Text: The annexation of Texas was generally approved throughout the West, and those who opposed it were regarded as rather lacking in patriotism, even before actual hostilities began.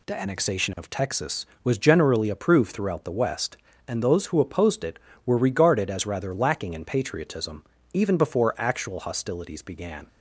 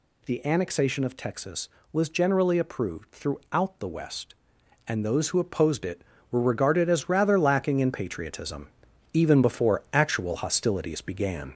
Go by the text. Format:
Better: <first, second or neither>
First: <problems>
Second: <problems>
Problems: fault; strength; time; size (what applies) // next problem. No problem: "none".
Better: first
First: none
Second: gets louder; noticeable; throughout; 5 dB